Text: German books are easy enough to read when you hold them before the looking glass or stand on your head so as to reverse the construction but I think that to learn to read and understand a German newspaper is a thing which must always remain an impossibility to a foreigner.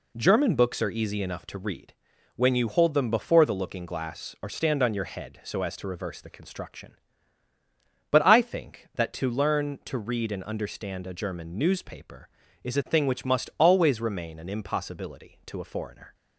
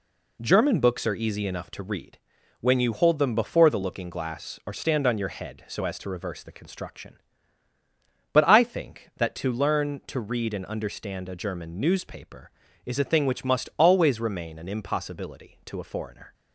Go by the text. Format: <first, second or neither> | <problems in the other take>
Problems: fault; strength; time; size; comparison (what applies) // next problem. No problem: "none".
neither | pauses between "read" and "when"; the same in both